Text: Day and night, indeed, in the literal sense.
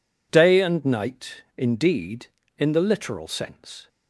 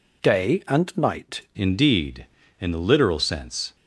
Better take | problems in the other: first | changes voice at "indeed"; from 1.5 s on; 2.2 s long

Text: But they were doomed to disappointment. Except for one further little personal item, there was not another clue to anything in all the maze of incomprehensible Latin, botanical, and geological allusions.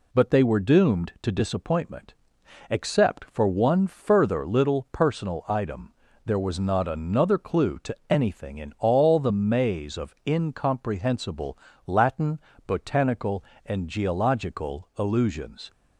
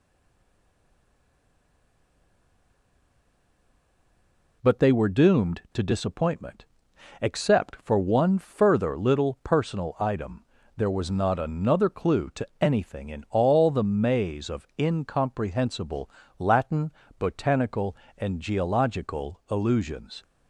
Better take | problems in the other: first | stays silent before the first word; strong; until 4.6 s; 4.6 s long // pauses between "incomprehensible" and "Latin"; slight; at 16.0 s; 0.30 s long; slight in the first

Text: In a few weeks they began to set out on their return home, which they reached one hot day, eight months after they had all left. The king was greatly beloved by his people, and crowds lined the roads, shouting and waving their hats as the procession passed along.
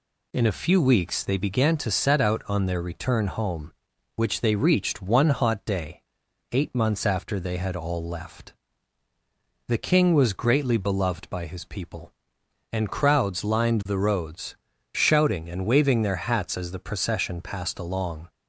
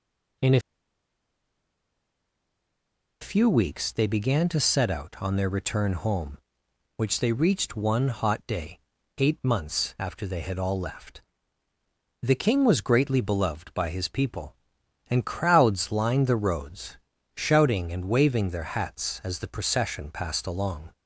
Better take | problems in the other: first | pauses between "a" and "few"; strong; at 0.6 s; 2.6 s long

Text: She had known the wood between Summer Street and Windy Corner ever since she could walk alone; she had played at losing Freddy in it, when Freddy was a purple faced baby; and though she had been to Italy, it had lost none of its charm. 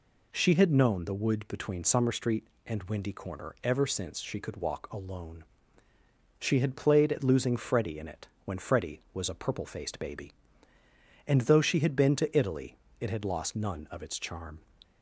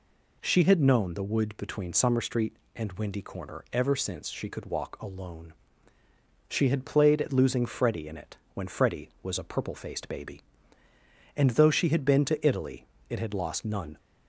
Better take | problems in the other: first | stops before "of its charm"; at 13.9 s

